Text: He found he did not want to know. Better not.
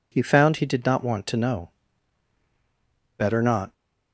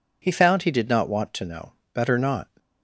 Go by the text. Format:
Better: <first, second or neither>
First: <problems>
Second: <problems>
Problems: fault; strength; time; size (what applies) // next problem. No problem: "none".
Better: neither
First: none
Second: none